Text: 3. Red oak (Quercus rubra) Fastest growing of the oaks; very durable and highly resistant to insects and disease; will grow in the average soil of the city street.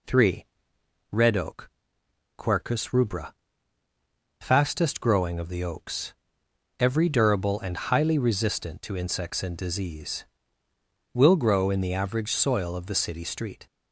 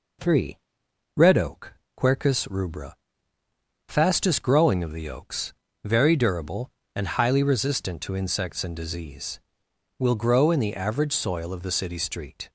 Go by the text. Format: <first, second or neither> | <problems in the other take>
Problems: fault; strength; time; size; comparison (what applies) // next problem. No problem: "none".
second | says "every" for "very"; at 6.7 s